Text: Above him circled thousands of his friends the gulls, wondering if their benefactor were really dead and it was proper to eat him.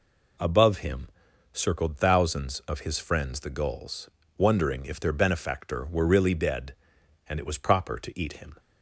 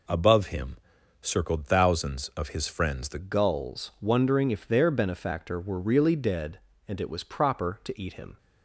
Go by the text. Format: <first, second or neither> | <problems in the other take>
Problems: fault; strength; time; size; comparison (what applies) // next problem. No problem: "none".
first | pauses between "him" and "circled"; noticeable; at 0.7 s; 0.46 s long; noticeable in the first // changes voice at "gulls"; from 3.1 s on; 5.2 s long